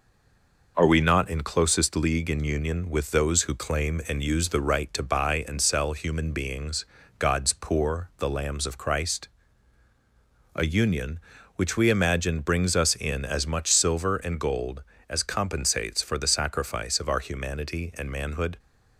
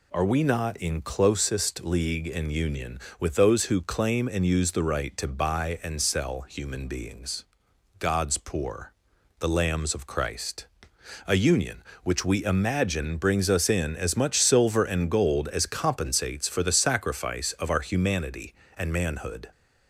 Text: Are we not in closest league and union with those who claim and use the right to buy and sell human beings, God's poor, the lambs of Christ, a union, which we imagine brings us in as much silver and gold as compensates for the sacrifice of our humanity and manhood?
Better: second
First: stays silent before the first word; slight; until 0.7 s; 0.7 s long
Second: none

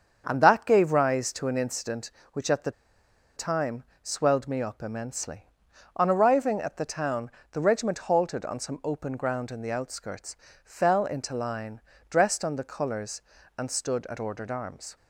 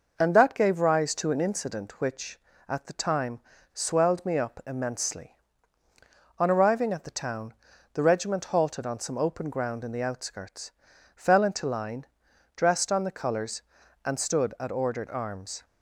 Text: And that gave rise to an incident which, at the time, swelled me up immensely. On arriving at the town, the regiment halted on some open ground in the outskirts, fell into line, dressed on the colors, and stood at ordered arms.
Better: second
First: starts louder than the rest; strong; until 1.2 s; 7 dB // pauses between "the" and "time"; noticeable; at 2.7 s; 0.65 s long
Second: none

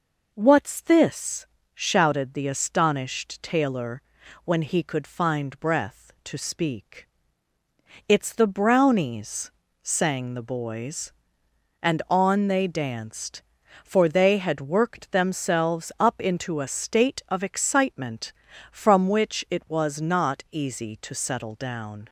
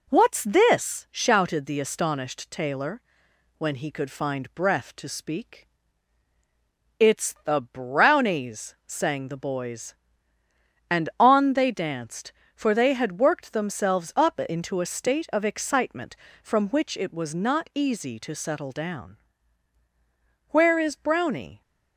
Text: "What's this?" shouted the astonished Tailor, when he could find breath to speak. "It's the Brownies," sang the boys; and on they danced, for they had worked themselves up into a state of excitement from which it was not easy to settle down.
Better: first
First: none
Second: goes on to say "Where is Brownie"; noticeable; from 20.5 s on; 1.1 s long

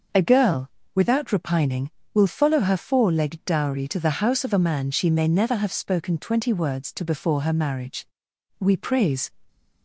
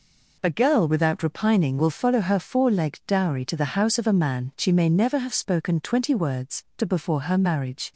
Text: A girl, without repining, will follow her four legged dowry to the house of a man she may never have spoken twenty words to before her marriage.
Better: second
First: starts louder than the rest; noticeable; until 1.4 s; 6 dB // goes on to say "We praise"; noticeable; from 8.5 s on; 0.72 s long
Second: none

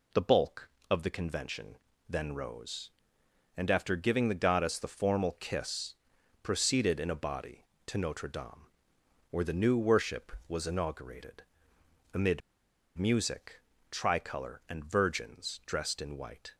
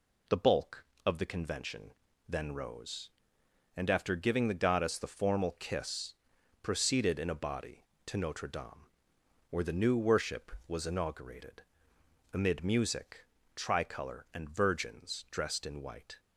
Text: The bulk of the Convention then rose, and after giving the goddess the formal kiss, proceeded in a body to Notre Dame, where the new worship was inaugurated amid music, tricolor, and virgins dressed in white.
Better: second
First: pauses between "Convention" and "then"; slight; at 1.7 s; 0.32 s long // pauses between "inaugurated" and "amid"; noticeable; at 11.4 s; 0.70 s long // pauses between "amid" and "music"; noticeable; at 12.4 s; 0.56 s long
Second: pauses between "Convention" and "then"; slight; at 1.9 s; 0.36 s long // pauses between "inaugurated" and "amid"; noticeable; at 11.6 s; 0.70 s long

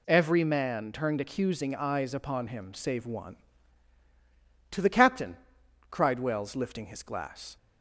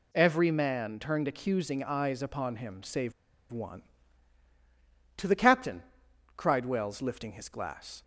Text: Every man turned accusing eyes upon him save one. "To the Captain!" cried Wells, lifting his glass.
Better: first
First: none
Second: pauses between "save" and "one"; at 3.1 s; 0.39 s long

